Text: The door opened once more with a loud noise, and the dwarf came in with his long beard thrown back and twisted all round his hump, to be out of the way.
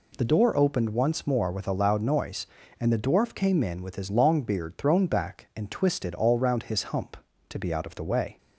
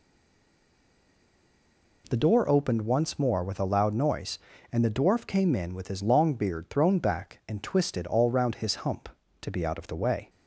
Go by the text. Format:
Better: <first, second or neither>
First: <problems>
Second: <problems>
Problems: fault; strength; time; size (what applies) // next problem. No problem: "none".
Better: first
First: none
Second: stays silent before the first word; noticeable; until 2.0 s; 2.0 s long